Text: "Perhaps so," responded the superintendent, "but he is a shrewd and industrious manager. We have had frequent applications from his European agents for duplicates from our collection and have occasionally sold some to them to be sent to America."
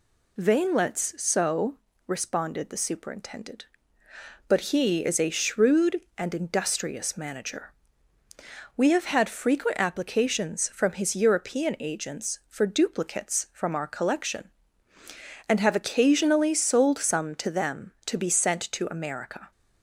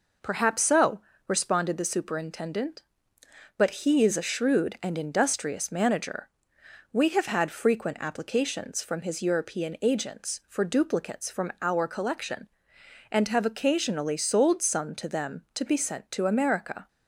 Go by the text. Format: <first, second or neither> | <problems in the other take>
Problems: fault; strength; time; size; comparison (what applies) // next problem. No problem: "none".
second | says "Veinlets" for "Perhaps"; at 0.3 s